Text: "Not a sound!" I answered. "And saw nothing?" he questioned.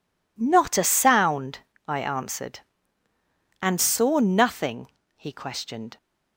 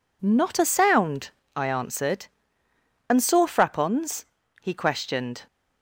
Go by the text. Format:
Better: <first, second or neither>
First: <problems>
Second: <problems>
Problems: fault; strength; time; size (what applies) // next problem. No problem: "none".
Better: first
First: none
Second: says "frappons" for "nothing"; at 3.4 s